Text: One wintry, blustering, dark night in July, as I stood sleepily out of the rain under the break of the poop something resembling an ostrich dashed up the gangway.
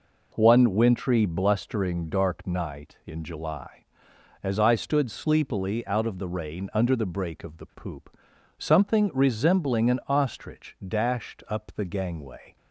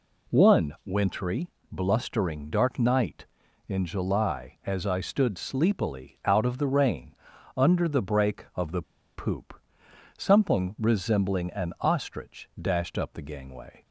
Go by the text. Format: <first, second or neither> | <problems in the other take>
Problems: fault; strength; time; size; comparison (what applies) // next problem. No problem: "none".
first | pauses between "rain" and "under"; at 7.1 s; 0.42 s long // pauses between "the" and "poop"; slight; at 8.8 s; 0.33 s long // pauses between "poop" and "something"; noticeable; at 9.5 s; 0.66 s long; also in the first